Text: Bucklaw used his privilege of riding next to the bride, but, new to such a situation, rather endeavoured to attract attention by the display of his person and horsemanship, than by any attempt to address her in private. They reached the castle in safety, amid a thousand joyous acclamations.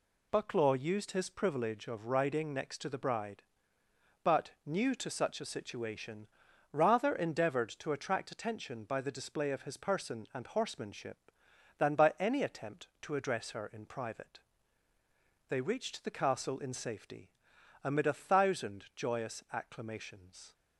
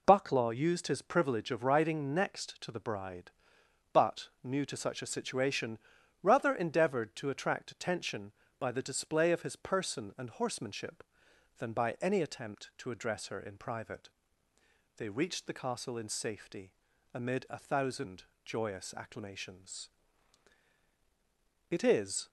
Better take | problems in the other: first | pauses between "thousand" and "joyous"; slight; at 18.2 s; 0.20 s long // goes on to say "It is"; from 21.7 s on; 0.58 s long

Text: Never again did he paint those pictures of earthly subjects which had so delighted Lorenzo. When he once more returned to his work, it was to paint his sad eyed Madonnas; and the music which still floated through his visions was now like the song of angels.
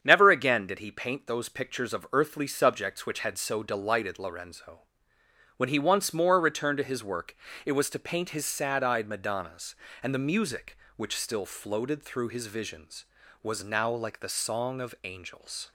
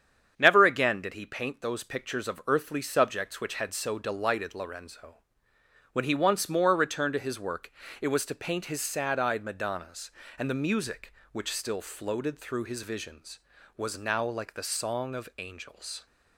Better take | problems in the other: neither | starts louder than the rest; strong; the same in both

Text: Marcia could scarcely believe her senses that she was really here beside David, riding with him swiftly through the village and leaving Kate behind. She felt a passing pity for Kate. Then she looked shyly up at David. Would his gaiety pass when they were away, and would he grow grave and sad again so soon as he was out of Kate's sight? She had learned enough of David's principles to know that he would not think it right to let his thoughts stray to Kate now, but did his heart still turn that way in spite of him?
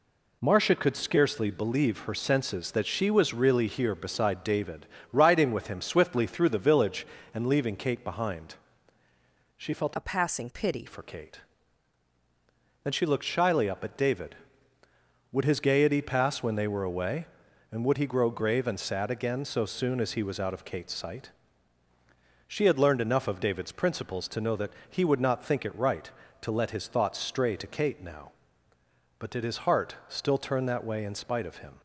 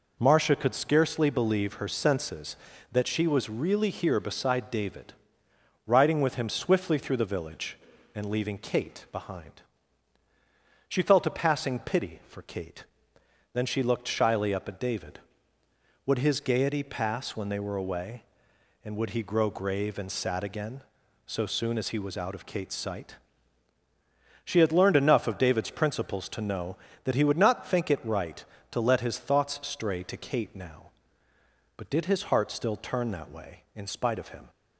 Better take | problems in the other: second | changes voice from "a" to "pity"; from 9.9 to 10.8 s; 0.9 s long // pauses between "that" and "he"; slight; at 24.7 s; 0.16 s long

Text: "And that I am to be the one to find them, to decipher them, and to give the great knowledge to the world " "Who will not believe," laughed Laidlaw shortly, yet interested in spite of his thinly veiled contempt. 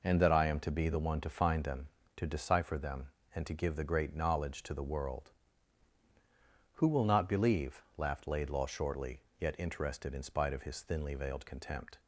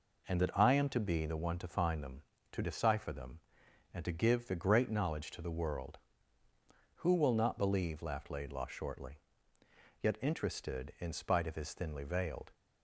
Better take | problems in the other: first | stops before "contempt"; at 12.5 s

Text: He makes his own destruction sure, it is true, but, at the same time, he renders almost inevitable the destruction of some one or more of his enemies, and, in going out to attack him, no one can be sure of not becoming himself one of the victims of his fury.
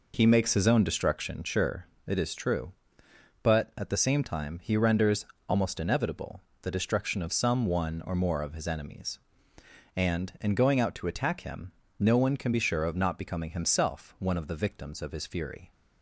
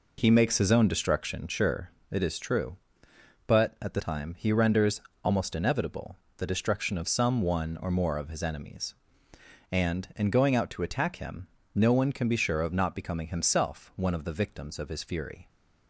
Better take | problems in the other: first | skips "same"; at 3.9 s // pauses between "renders" and "almost"; slight; at 5.0 s; 0.24 s long; slight in the first // pauses between "inevitable" and "the"; slight; at 6.1 s; 0.22 s long; slight in the first

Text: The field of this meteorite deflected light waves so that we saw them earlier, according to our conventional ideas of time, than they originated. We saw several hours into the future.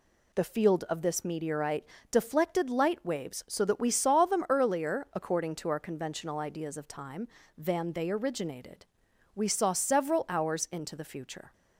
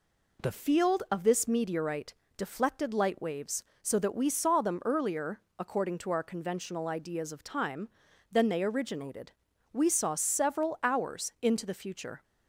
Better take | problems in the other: neither | pauses between "meteorite" and "deflected"; slight; the same in both

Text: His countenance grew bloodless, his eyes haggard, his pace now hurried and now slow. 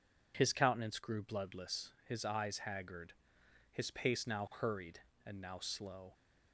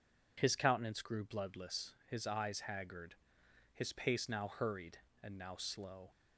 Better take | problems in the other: neither | none

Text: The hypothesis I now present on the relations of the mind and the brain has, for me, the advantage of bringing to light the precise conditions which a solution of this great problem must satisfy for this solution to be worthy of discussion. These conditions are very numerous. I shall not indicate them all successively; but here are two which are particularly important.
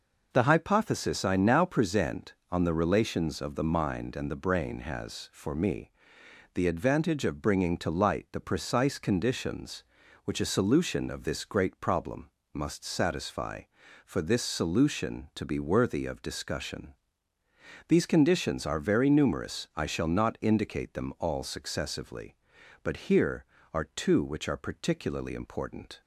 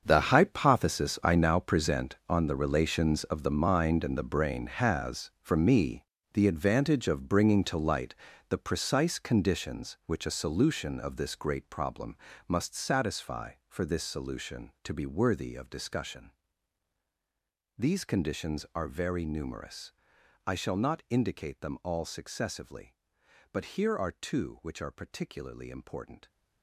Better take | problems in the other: first | gets quieter; strong; throughout; 14.5 dB // pauses between "light" and "the"; slight; at 8.1 s; 0.36 s long // pauses between "problem" and "must"; slight; at 12.1 s; 0.30 s long; slight in the first

